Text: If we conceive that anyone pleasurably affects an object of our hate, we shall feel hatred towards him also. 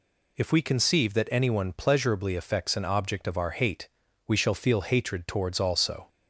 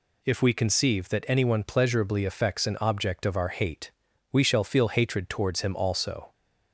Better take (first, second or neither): second